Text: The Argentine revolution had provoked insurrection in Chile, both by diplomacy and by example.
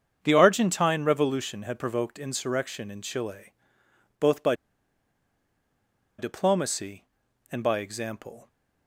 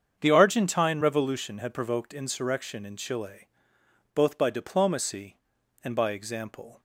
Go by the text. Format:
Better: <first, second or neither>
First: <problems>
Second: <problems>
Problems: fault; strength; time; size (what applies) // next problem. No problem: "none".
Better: second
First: starts louder than the rest; strong; until 1.2 s; 7.5 dB // pauses between "by" and "diplomacy"; strong; at 4.5 s; 1.6 s long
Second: starts louder than the rest; strong; until 1.2 s; 7.5 dB